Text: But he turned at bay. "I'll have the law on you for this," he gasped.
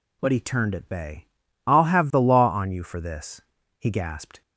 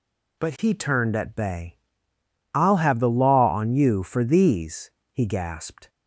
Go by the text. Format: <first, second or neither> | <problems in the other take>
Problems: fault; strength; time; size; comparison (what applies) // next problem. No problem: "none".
first | says "these" for "this"; at 4.2 s